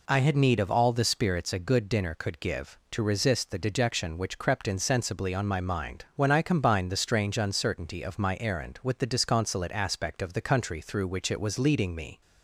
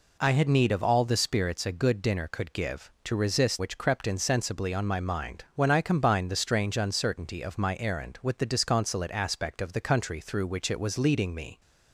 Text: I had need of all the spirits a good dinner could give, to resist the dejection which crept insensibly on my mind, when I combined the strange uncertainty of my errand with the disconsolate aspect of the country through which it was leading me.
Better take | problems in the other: first | skips "the dejection"; at 3.5 s

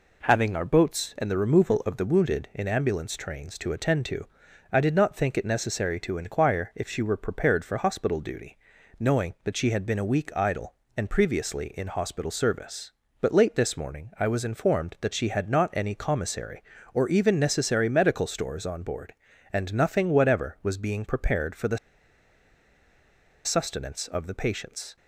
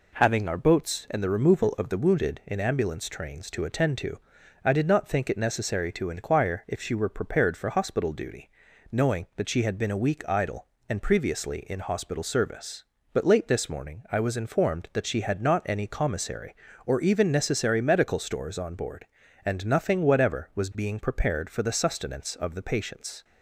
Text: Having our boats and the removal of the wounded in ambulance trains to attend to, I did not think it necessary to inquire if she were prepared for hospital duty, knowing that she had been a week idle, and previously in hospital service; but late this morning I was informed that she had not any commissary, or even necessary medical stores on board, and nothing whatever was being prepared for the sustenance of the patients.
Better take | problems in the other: second | pauses between "the" and "sustenance"; strong; at 21.7 s; 1.6 s long

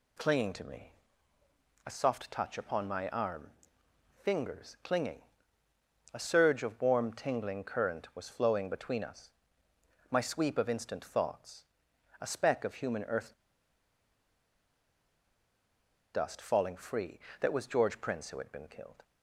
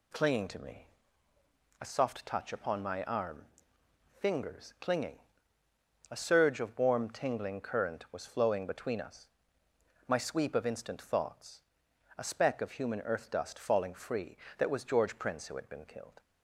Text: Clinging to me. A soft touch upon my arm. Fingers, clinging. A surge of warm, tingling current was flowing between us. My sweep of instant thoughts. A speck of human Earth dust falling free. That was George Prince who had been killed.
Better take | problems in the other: second | pauses between "Earth" and "dust"; strong; at 13.3 s; 2.8 s long

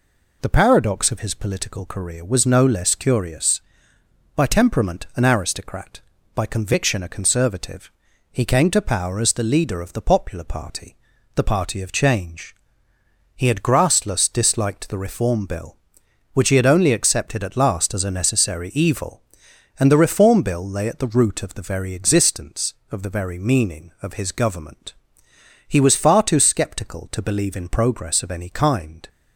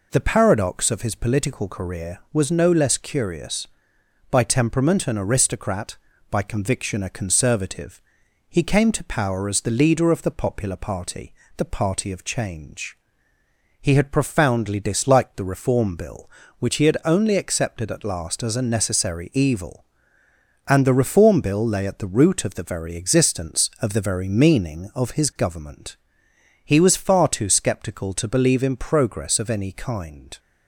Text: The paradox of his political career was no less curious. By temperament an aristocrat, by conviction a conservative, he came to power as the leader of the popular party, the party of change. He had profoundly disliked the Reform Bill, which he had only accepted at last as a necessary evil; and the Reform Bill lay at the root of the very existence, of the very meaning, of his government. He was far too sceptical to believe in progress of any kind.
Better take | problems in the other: second | says "grassless" for "profoundly"; at 13.6 s

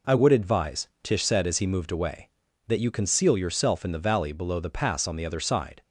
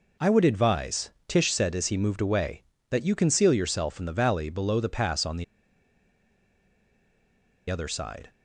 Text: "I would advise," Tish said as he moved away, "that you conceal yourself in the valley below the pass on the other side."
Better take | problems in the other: first | pauses between "the" and "other"; strong; at 5.4 s; 2.2 s long

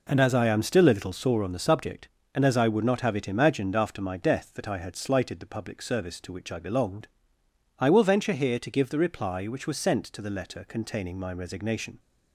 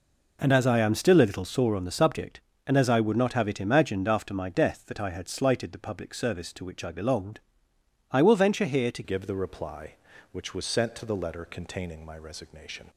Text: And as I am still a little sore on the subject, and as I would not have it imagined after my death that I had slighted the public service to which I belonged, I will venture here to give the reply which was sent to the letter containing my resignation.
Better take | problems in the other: first | changes voice at "give"; from 9.0 s on; 3.8 s long

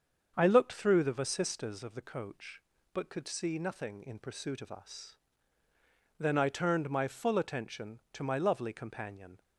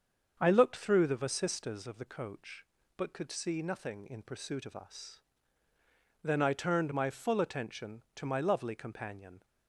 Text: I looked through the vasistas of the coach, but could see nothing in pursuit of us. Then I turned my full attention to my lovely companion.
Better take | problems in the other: neither | starts louder than the rest; the same in both

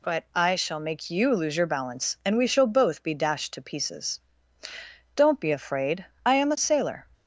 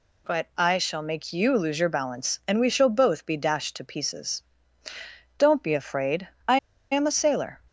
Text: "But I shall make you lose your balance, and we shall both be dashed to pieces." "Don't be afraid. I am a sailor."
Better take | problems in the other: first | pauses between "I" and "am"; slight; at 6.5 s; 0.34 s long

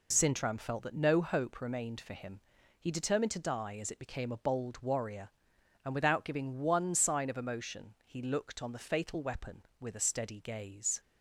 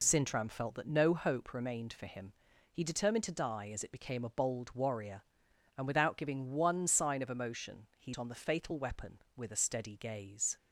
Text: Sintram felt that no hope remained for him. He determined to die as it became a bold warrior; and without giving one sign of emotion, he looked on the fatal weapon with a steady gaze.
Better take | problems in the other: first | skips "looked"; at 8.1 s

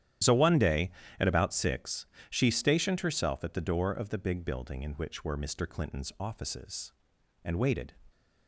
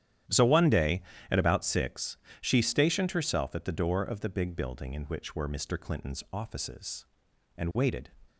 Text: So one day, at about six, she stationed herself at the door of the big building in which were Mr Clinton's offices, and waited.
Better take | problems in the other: second | loses the start of "So"; at 0.2 s; 45 ms // starts louder than the rest; strong; until 1.5 s; 11 dB; strong in the second

